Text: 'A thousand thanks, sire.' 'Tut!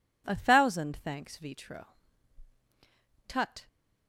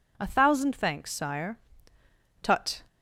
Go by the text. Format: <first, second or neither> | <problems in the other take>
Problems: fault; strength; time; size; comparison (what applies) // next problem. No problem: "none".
second | says "vitro" for "sire"; at 1.3 s